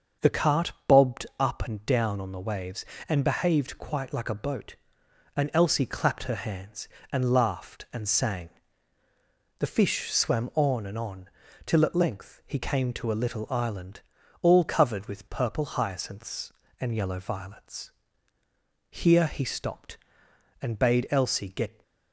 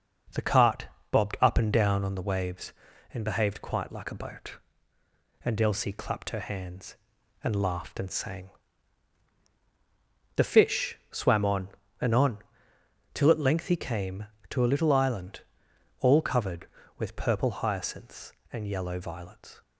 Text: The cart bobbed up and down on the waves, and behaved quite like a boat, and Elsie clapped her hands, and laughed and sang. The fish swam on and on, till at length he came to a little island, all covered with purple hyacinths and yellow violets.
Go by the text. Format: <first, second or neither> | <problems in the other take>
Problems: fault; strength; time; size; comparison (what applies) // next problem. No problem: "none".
second | starts louder than the rest; until 1.4 s; 6.5 dB // pauses between "cart" and "bobbed"; slight; at 0.7 s; 0.16 s long; slight in the second // goes on to say "Here he stopped and bade Elsie get"; strong; from 18.9 s on; 2.9 s long